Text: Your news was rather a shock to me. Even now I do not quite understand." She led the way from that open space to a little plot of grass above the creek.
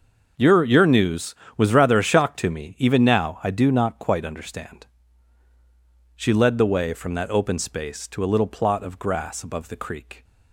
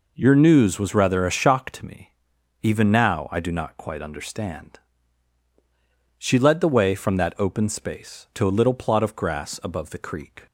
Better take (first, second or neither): second